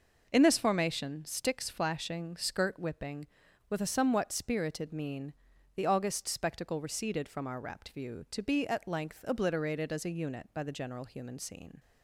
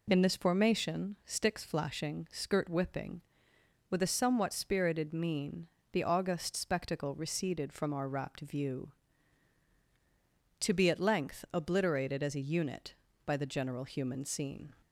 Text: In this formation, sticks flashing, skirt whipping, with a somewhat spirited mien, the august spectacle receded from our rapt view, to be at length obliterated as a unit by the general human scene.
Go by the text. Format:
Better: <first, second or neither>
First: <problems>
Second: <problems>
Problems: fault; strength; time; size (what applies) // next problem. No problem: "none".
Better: neither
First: none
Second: none